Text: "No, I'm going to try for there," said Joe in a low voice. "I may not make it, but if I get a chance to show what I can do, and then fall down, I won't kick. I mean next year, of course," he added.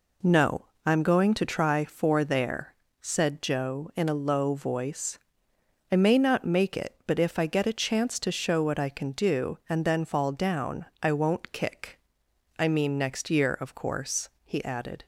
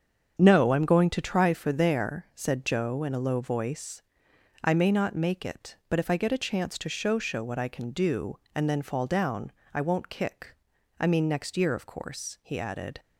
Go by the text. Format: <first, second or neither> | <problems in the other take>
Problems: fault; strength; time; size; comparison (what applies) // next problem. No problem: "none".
first | starts louder than the rest; strong; until 1.4 s; 7 dB // says "show" twice; at 7.1 s